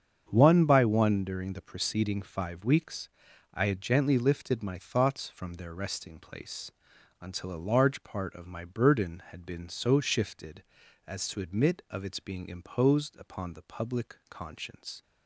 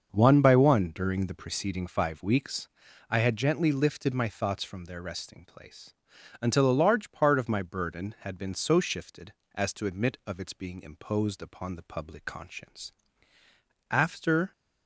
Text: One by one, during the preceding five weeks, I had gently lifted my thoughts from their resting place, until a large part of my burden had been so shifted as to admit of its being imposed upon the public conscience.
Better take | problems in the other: first | starts louder than the rest; until 1.1 s; 6.5 dB; strong in the first // goes on to say "After"; noticeable; from 13.8 s on; 0.62 s long

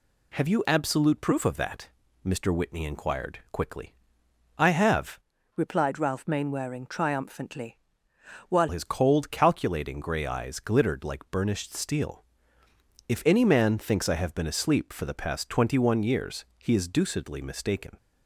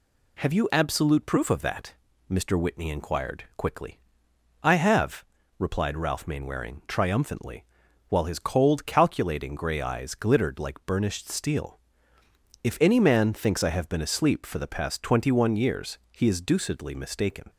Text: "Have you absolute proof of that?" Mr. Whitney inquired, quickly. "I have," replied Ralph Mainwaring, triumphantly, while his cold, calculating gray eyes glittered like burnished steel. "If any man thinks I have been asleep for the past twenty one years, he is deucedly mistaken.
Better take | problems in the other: second | changes voice from "replied" to "while"; from 5.5 to 8.6 s; 3.1 s long

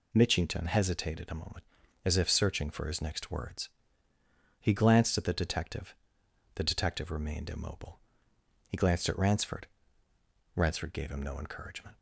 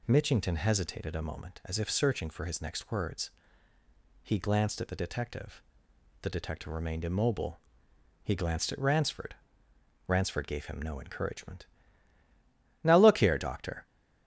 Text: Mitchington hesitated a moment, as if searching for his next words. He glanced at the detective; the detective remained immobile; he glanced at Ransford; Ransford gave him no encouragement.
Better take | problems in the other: first | goes on to say "Now look here doctor"; noticeable; from 12.8 s on; 1.0 s long

